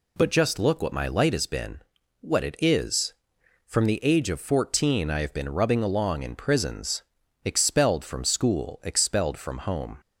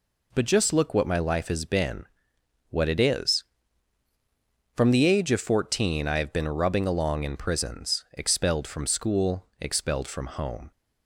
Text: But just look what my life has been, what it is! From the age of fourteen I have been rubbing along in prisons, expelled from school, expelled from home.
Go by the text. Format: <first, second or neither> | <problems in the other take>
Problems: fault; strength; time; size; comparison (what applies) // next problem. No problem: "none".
second | says "light" for "life"; at 1.0 s